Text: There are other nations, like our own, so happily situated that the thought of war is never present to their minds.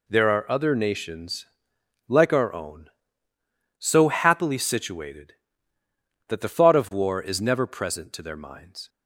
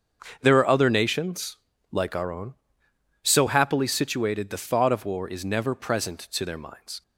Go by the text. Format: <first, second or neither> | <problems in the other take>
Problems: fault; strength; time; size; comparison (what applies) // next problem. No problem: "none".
first | starts louder than the rest; until 1.4 s; 6.5 dB // skips "that"; at 4.4 s